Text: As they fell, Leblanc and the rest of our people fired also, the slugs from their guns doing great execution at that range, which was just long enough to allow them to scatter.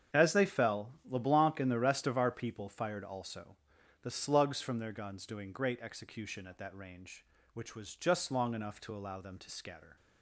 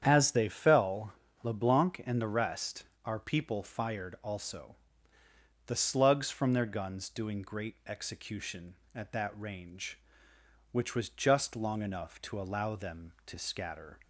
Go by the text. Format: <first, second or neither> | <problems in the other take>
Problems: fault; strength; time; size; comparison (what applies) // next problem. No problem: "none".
first | starts louder than the rest; strong; until 1.0 s; 8.5 dB; strong in the first // skips "of"; at 2.9 s